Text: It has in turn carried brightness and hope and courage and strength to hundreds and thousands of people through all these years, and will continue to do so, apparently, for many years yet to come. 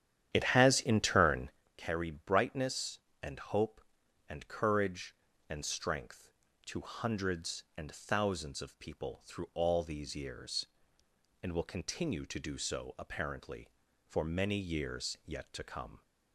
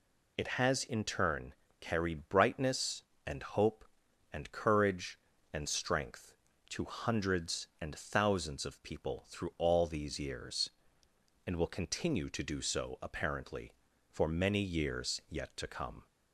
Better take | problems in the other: second | starts louder than the rest; strong; until 1.6 s; 10 dB // pauses between "turn" and "carried"; slight; at 1.4 s; 0.28 s long; slight in the second

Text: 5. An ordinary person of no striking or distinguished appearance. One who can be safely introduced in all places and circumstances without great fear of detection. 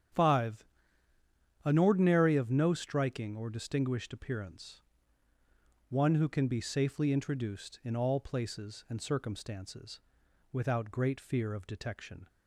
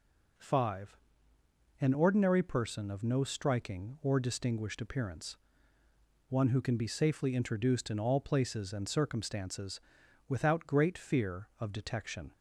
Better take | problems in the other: second | starts louder than the rest; strong; until 2.1 s; 8.5 dB // skips "person"; at 2.3 s // pauses between "circumstances" and "without"; noticeable; at 10.0 s; 0.50 s long; noticeable in the second

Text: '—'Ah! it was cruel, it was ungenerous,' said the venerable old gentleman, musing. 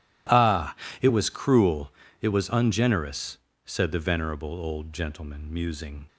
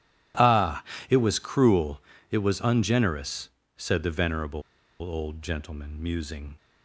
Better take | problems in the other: first | pauses between "venerable" and "old"; at 4.5 s; 0.40 s long

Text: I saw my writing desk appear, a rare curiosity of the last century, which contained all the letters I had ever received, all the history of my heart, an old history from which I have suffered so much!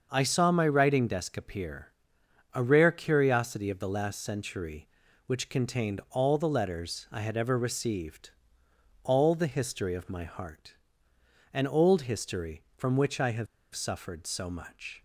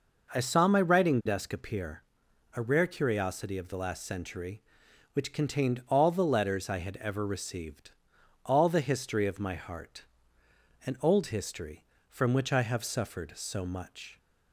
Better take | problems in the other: second | starts louder than the rest; until 1.1 s; 6.5 dB // pauses between "have" and "suffered"; slight; at 13.4 s; 0.27 s long

